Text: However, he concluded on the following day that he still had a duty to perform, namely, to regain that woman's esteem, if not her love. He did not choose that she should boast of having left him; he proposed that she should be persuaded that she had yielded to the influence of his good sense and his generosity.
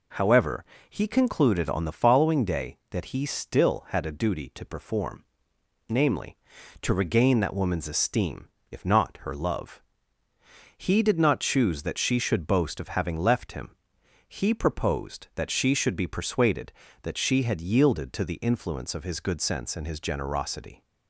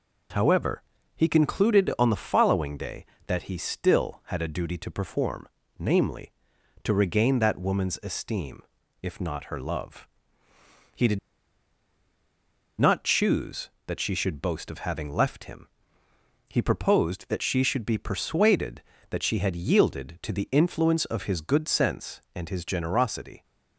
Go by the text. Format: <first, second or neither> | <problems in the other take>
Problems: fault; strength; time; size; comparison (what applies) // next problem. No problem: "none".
first | pauses between "did" and "not"; strong; at 11.1 s; 1.6 s long